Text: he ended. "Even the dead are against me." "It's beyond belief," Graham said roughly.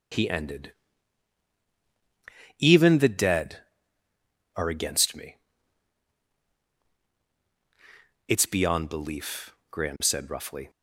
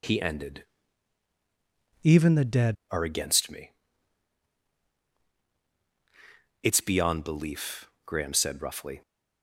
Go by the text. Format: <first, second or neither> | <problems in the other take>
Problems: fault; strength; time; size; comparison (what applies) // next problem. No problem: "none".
first | changes voice from "Even" to "dead"; from 2.0 to 2.7 s; 0.7 s long